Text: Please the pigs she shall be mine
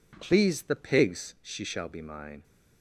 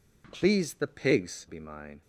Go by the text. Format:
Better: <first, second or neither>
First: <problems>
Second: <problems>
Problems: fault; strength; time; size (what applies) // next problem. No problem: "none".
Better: first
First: none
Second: skips "she shall"; at 1.4 s